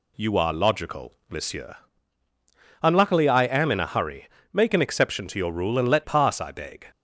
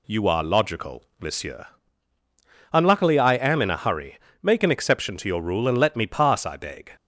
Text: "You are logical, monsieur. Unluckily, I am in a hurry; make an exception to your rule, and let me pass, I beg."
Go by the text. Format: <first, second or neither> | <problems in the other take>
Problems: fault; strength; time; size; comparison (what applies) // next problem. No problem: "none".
second | skips "me"; at 6.0 s